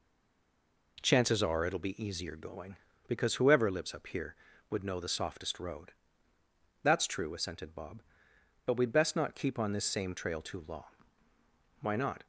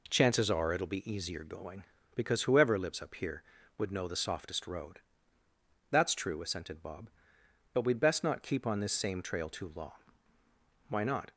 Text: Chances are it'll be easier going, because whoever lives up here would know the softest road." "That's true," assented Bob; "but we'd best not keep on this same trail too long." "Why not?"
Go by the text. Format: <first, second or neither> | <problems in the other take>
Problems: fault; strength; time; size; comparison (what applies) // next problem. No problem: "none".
second | stays silent before the first word; slight; until 0.9 s; 0.9 s long